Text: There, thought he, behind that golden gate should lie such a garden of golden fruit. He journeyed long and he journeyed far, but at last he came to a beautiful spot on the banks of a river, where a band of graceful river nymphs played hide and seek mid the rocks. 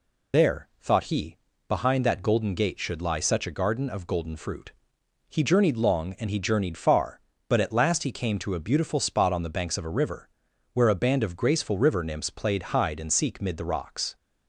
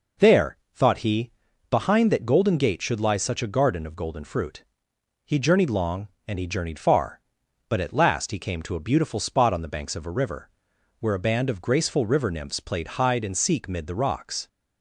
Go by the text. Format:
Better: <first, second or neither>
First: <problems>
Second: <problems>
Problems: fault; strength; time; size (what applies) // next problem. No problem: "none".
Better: second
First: loses the start of "There"; at 0.3 s; 85 ms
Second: none